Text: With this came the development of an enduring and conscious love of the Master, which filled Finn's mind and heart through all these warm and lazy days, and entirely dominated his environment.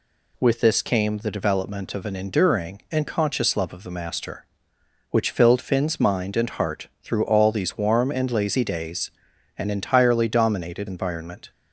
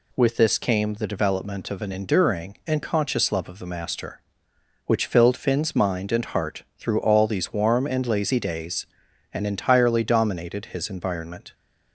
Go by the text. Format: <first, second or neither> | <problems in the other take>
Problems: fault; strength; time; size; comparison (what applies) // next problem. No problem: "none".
second | skips "his"; at 10.8 s